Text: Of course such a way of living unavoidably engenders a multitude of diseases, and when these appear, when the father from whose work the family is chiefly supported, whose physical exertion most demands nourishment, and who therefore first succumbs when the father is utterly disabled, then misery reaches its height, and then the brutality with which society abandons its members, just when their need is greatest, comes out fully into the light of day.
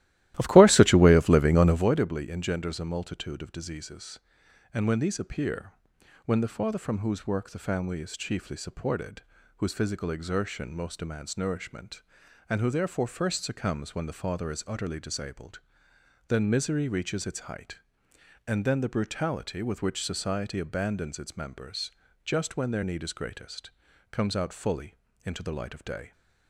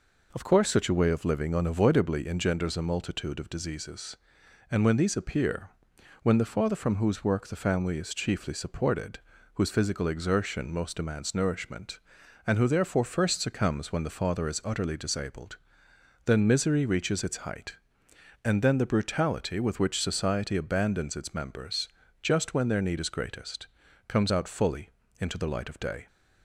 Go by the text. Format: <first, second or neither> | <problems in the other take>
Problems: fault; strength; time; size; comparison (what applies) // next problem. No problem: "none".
second | starts louder than the rest; strong; until 1.9 s; 15 dB // pauses between "fully" and "into"; slight; at 24.9 s; 0.28 s long; slight in the second